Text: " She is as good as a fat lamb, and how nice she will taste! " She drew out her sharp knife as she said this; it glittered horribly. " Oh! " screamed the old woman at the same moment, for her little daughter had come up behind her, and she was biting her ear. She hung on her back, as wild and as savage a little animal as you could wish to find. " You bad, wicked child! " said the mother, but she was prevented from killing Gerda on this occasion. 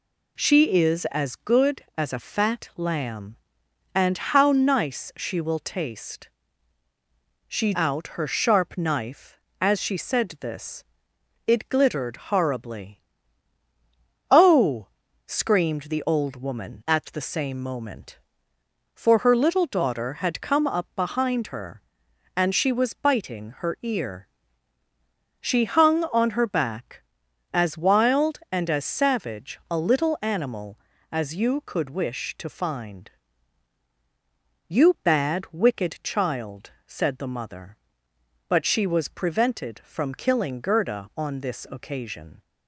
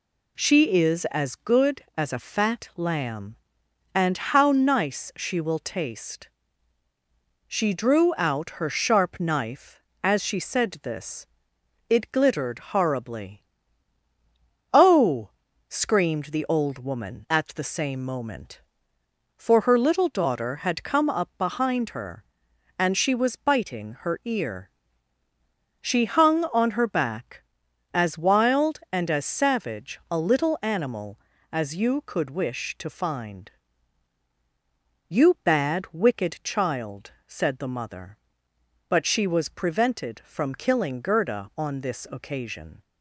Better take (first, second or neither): second